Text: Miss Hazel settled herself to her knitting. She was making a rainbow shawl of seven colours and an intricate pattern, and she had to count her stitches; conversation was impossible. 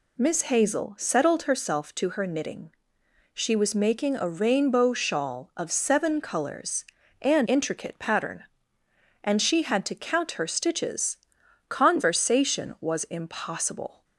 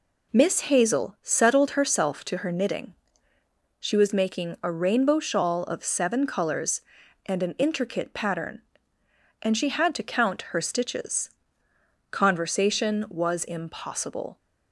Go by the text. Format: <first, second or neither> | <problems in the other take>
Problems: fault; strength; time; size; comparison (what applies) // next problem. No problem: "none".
second | skips "an"; at 7.4 s